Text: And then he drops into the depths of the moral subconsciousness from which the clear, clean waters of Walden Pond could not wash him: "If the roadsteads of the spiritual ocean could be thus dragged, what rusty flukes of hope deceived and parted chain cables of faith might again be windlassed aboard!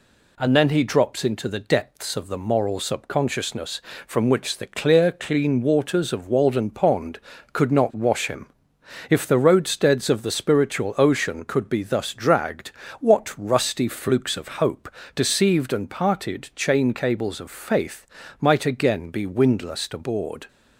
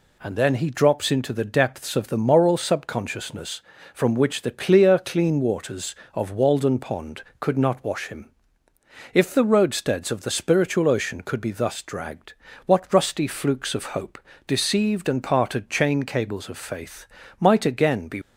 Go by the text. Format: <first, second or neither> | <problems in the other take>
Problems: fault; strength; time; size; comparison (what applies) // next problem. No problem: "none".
first | pauses between "hope" and "deceived"; slight; at 14.1 s; 0.30 s long; slight in the first // pauses between "faith" and "might"; slight; at 17.0 s; 0.34 s long; slight in the first // stops before "windlassed aboard"; at 18.2 s